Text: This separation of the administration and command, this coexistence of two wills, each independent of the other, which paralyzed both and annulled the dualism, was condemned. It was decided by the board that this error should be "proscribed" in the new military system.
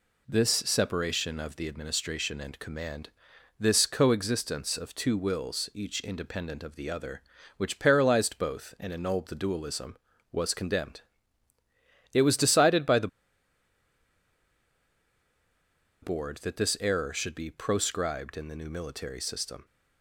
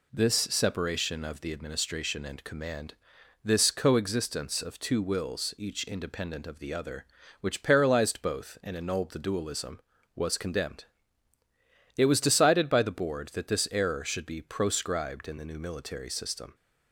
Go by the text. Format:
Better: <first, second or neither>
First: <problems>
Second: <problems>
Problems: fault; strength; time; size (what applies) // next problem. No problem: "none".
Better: second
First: pauses between "the" and "board"; strong; at 13.0 s; 2.9 s long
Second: none